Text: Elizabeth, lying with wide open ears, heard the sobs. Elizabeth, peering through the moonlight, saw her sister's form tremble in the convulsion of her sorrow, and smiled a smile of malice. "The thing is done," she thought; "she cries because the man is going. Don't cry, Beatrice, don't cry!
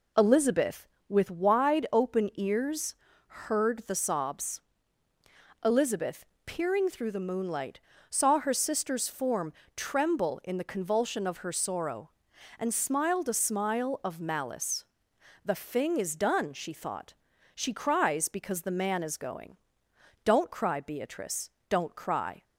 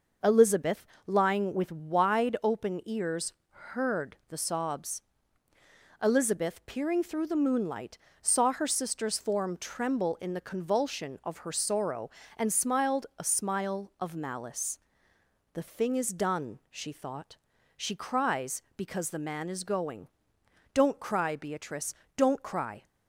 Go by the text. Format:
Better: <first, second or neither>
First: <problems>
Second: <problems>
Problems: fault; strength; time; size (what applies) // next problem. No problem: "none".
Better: second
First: skips "lying"; at 0.9 s // pauses between "form" and "tremble"; slight; at 9.5 s; 0.24 s long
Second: none